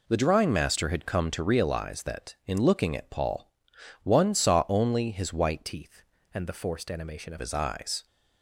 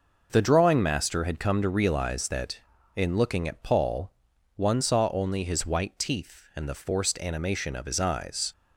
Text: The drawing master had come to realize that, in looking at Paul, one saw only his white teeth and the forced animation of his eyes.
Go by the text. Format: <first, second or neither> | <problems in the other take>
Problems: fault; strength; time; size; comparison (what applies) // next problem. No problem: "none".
second | changes voice from "teeth" to "of"; from 5.6 to 7.3 s; 1.7 s long